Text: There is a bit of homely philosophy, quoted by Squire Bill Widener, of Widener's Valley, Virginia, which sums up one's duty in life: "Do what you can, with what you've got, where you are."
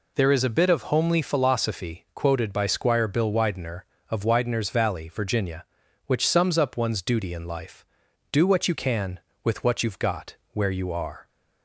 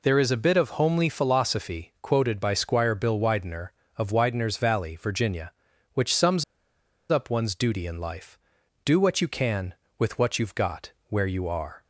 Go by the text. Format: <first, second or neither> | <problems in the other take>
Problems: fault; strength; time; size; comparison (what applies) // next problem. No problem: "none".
first | pauses between "sums" and "up"; noticeable; at 6.4 s; 0.67 s long